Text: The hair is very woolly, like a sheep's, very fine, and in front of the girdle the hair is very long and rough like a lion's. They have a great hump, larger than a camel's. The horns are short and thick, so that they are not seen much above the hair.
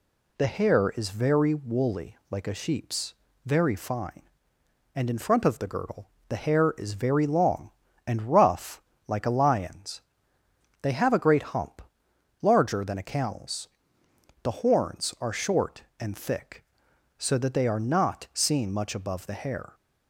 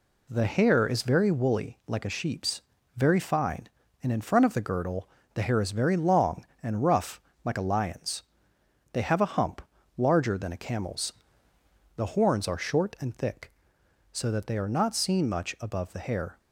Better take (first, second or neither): first